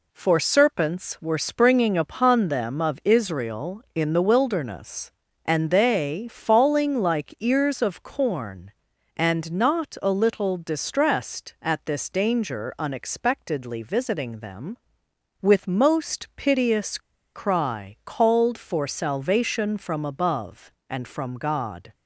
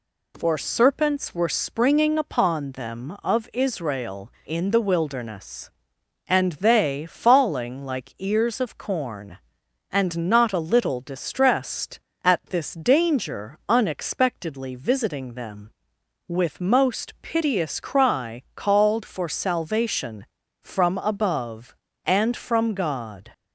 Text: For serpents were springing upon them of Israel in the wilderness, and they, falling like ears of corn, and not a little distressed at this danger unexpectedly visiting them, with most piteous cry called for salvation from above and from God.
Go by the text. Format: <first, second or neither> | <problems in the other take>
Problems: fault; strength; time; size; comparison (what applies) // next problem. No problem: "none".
second | pauses between "piteous" and "cry"; at 16.9 s; 0.36 s long